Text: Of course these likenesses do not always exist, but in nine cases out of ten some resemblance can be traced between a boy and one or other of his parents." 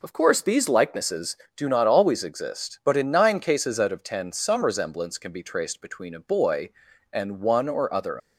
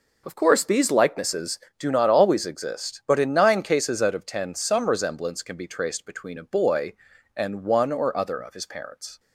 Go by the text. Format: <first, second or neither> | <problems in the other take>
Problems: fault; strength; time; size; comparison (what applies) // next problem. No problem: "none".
second | stops before "of his parents"; at 8.1 s